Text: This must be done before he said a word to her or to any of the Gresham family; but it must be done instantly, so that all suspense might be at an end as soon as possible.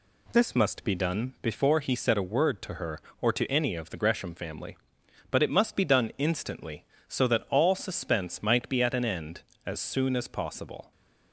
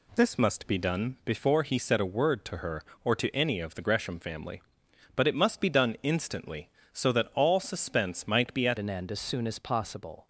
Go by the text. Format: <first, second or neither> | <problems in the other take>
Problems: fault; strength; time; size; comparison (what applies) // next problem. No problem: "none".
first | changes voice at "an"; from 8.7 s on; 1.5 s long